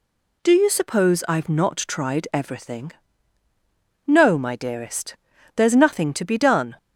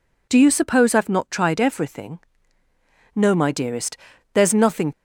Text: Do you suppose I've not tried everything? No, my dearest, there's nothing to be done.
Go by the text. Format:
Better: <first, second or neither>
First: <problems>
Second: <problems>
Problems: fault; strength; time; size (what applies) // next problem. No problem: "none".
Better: first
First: none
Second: stops before "to be done"; at 4.9 s